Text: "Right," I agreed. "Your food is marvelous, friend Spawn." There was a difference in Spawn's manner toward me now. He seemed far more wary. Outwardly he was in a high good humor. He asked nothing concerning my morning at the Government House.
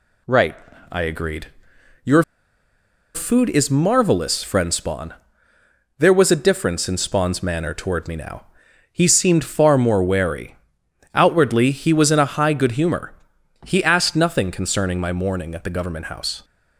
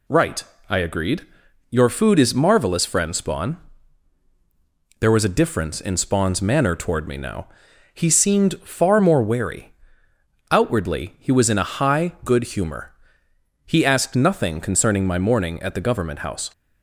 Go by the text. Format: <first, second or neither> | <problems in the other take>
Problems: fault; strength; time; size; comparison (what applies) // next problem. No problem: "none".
second | pauses between "Your" and "food"; noticeable; at 2.2 s; 0.91 s long